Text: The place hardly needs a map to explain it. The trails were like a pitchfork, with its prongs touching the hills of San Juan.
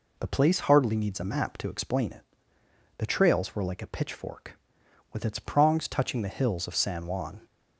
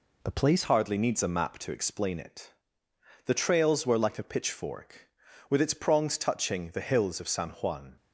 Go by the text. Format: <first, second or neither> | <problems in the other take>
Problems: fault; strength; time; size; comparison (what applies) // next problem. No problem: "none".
first | changes voice at "hardly"; from 0.6 s on; 7.3 s long